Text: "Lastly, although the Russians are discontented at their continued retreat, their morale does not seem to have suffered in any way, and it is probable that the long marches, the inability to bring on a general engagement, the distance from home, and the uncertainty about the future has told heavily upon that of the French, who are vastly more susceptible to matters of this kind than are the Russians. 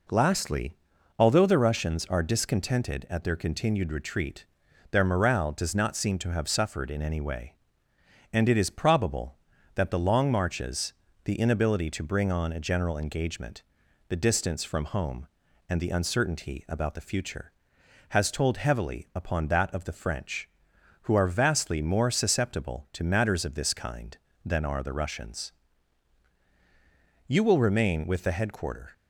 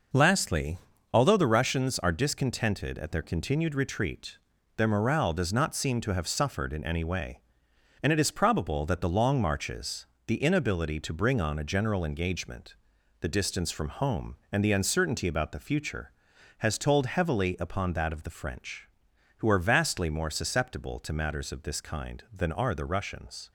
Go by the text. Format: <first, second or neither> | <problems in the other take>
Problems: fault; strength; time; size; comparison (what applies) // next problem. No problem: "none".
second | goes on to say "You will remain with the headquarter"; from 27.2 s on; 1.6 s long